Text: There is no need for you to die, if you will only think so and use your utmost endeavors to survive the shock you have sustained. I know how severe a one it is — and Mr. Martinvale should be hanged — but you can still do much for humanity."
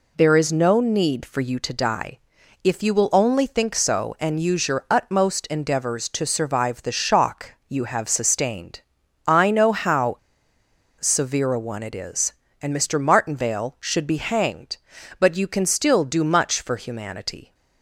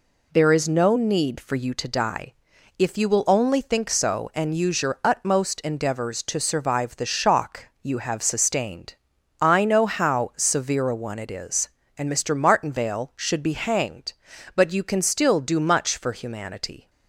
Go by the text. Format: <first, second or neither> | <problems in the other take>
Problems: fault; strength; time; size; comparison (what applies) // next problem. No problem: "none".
second | pauses between "how" and "severe"; noticeable; at 10.1 s; 0.81 s long